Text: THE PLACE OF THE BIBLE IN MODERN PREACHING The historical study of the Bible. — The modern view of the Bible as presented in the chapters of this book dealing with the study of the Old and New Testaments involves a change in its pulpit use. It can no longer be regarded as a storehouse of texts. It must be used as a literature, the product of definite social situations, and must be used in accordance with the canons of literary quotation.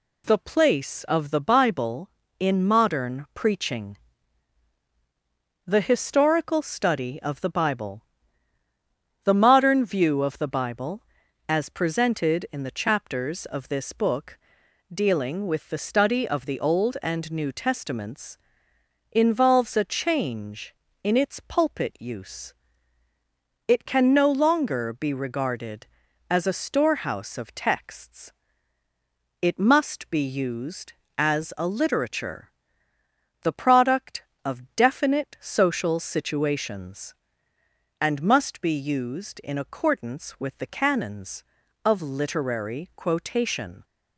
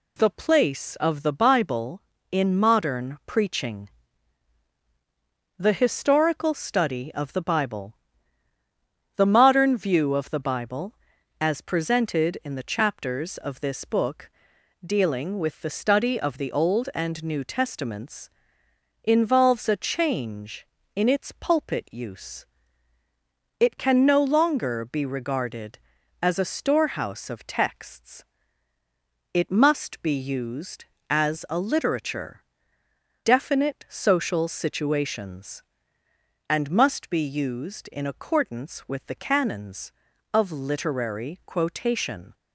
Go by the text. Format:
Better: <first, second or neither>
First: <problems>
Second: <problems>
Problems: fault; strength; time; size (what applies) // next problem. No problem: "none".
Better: first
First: pauses between "PREACHING" and "The"; strong; at 3.9 s; 1.7 s long // pauses between "book" and "dealing"; noticeable; at 14.3 s; 0.52 s long // pauses between "Testaments" and "involves"; noticeable; at 18.3 s; 0.72 s long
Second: pauses between "PREACHING" and "The"; strong; at 3.8 s; 1.7 s long // pauses between "book" and "dealing"; noticeable; at 14.3 s; 0.52 s long // pauses between "Testaments" and "involves"; noticeable; at 18.3 s; 0.72 s long // skips "the product of"; at 32.8 s